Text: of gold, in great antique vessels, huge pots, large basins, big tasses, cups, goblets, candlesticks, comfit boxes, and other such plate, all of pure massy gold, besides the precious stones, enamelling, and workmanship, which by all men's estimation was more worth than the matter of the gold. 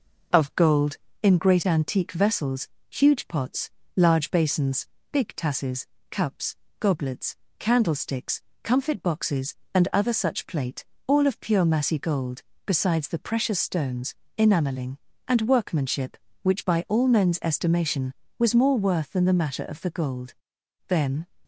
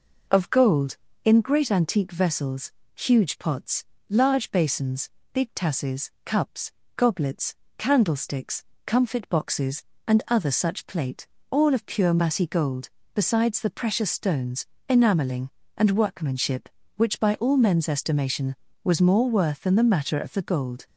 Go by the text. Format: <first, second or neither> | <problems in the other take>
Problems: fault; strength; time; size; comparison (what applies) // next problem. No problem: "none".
second | goes on to say "Then"; slight; from 20.8 s on; 0.38 s long